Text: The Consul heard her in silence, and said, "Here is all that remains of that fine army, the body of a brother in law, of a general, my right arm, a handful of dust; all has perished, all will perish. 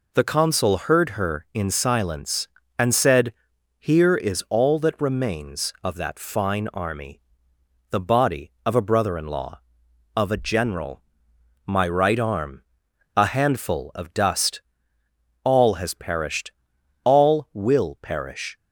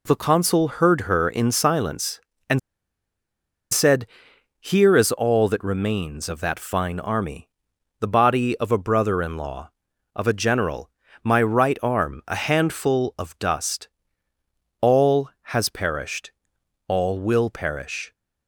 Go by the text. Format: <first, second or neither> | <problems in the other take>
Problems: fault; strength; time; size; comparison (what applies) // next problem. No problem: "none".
first | pauses between "and" and "said"; at 2.5 s; 1.1 s long